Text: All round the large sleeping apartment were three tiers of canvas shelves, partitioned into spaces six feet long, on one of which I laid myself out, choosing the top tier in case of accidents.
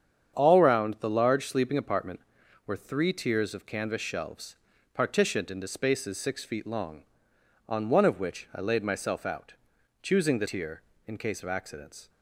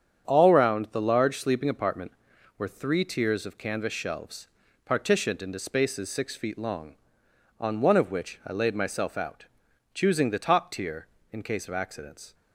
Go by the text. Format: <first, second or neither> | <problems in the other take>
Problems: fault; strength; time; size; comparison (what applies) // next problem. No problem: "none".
second | starts louder than the rest; strong; until 1.3 s; 8 dB; strong in the second // skips "top"; at 10.4 s